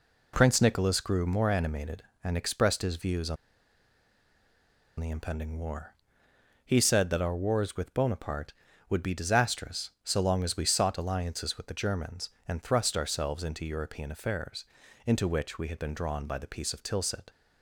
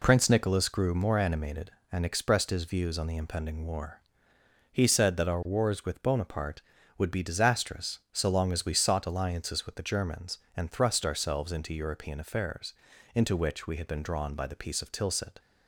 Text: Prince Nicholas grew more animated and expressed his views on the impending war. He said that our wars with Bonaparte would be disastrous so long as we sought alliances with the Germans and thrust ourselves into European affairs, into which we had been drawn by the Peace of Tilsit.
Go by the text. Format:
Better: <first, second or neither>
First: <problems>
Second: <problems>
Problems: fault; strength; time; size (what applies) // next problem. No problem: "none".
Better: second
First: pauses between "on" and "the"; strong; at 3.3 s; 1.6 s long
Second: none